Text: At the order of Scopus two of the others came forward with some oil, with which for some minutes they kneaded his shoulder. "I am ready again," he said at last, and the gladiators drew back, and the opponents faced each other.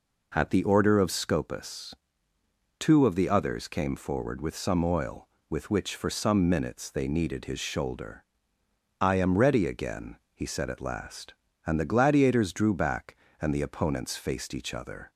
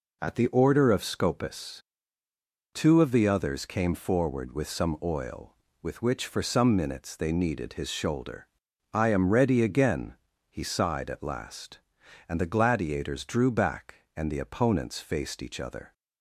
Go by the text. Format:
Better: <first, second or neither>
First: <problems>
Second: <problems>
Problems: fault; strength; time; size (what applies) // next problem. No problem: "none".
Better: first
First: pauses between "Scopus" and "two"; noticeable; at 1.9 s; 0.84 s long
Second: pauses between "Scopus" and "two"; noticeable; at 1.8 s; 0.92 s long // says "sighed" for "said"; at 10.6 s